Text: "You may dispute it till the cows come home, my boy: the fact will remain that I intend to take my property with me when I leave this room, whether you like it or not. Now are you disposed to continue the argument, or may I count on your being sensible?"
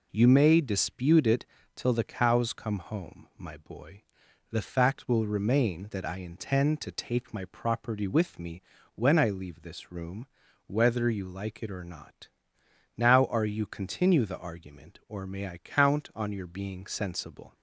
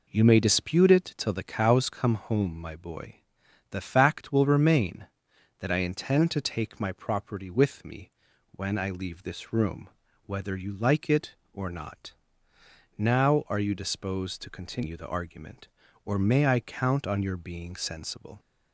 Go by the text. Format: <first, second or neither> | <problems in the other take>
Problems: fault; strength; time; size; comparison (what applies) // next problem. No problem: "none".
second | pauses between "it" and "till"; slight; at 1.4 s; 0.30 s long // pauses between "me" and "when"; slight; at 8.5 s; 0.36 s long; also in the second // skips "disposed to"; at 13.6 s